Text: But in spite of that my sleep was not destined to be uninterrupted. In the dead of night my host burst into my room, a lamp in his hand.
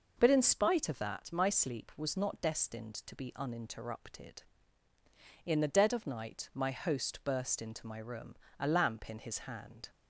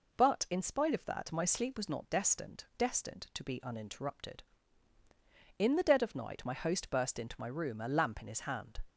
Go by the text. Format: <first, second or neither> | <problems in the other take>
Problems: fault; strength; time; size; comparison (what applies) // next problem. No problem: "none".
first | says "destined" twice; at 2.7 s